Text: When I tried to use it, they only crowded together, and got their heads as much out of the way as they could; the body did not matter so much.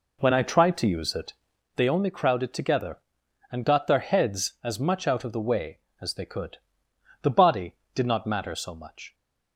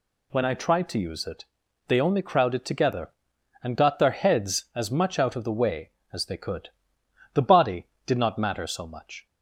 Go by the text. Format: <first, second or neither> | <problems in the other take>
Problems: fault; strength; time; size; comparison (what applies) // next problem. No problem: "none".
second | starts louder than the rest; until 1.6 s; 4 dB